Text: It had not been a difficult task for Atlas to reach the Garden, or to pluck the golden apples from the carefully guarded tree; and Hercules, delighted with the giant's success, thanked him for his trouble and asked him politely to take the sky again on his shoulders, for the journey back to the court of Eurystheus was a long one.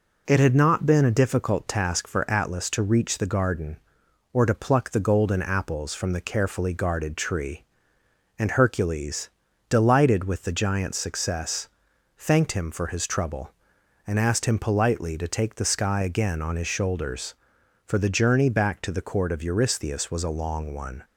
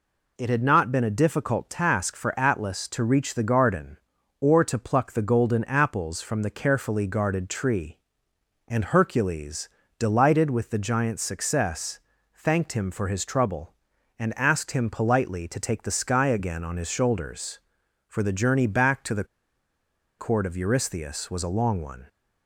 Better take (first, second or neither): first